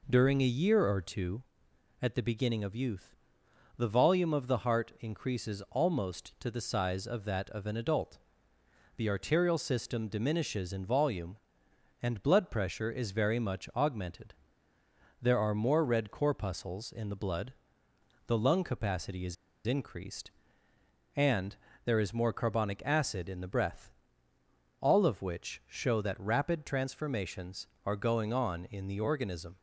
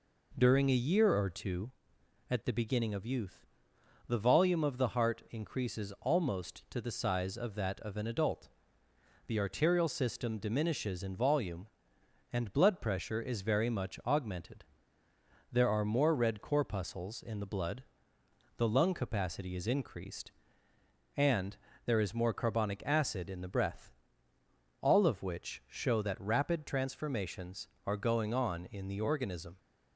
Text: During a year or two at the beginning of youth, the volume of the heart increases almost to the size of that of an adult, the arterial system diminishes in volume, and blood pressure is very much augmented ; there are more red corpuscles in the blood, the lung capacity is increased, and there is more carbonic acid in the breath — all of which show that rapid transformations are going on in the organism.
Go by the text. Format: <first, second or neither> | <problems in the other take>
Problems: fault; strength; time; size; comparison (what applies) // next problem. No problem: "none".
second | pauses between "is" and "increased"; slight; at 19.3 s; 0.32 s long // pauses between "and" and "there"; slight; at 21.5 s; 0.28 s long; slight in the second